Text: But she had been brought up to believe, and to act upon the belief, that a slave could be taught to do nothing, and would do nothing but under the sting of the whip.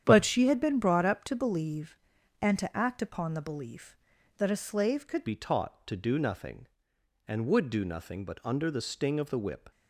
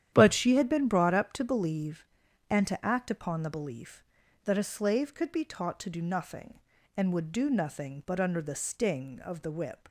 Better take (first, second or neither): second